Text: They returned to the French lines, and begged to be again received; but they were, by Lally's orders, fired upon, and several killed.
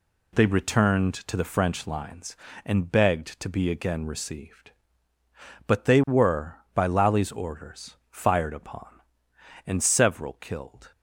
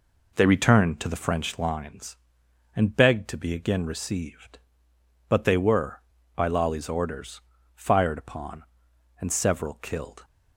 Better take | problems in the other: first | starts louder than the rest; until 1.5 s; 4 dB

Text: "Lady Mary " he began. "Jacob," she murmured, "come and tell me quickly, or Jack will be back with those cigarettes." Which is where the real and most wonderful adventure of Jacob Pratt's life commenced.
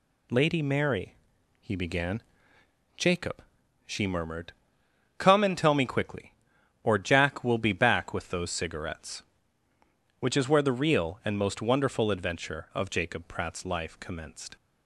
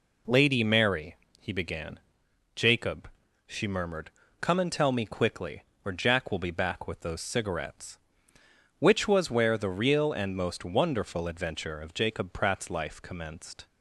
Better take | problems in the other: first | says "was" for "is"; at 9.0 s

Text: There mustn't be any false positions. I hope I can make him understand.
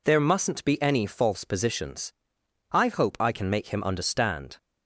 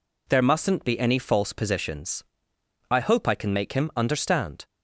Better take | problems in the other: neither | none

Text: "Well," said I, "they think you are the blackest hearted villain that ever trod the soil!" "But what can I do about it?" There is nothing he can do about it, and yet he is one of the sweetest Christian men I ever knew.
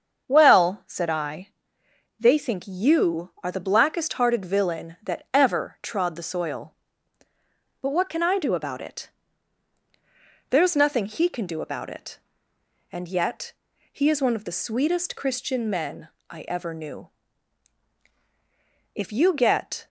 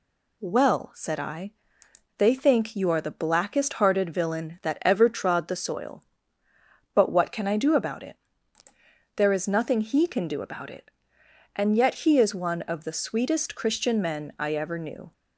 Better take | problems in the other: second | starts louder than the rest; until 1.2 s; 7 dB // pauses between "yet" and "he"; at 13.5 s; 0.40 s long // pauses between "men" and "I"; slight; at 16.0 s; 0.22 s long // goes on to say "If you get"; noticeable; from 18.9 s on; 0.92 s long

